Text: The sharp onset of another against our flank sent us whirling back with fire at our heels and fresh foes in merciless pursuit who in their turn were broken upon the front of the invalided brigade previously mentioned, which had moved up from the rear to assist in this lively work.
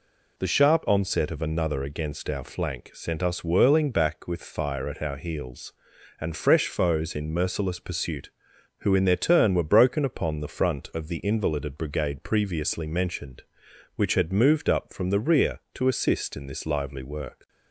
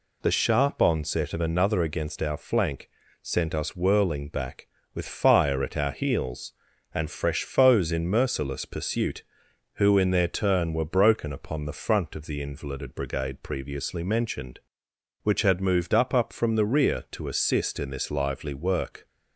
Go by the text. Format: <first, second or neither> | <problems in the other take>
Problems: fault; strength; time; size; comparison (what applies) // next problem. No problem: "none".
first | pauses between "flank" and "sent"; slight; at 2.9 s; 0.32 s long // says "up" twice; at 16.1 s